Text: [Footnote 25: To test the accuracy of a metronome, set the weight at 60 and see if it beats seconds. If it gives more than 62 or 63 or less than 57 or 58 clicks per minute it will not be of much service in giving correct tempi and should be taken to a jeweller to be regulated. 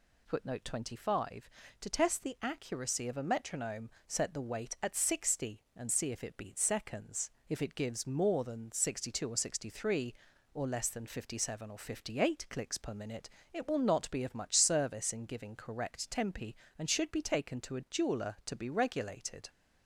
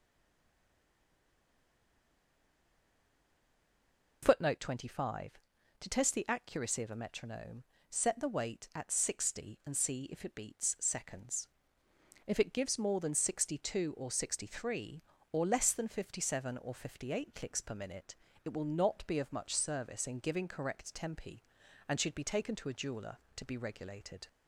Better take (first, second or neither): first